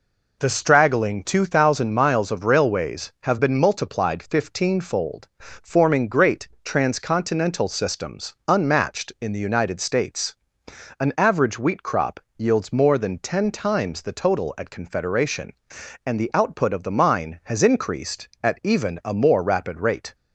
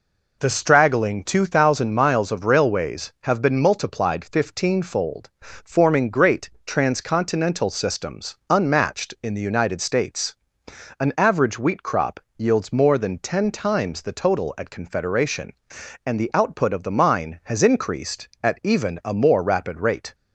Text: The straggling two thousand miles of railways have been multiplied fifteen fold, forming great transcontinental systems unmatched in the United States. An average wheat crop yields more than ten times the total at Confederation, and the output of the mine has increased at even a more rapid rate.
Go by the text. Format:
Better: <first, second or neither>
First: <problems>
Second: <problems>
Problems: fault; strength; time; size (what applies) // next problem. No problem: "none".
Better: neither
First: pauses between "great" and "transcontinental"; slight; at 6.4 s; 0.16 s long // pauses between "systems" and "unmatched"; slight; at 8.3 s; 0.16 s long // pauses between "crop" and "yields"; slight; at 12.1 s; 0.18 s long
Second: pauses between "great" and "transcontinental"; slight; at 6.5 s; 0.16 s long // pauses between "systems" and "unmatched"; slight; at 8.3 s; 0.16 s long // pauses between "crop" and "yields"; slight; at 12.1 s; 0.18 s long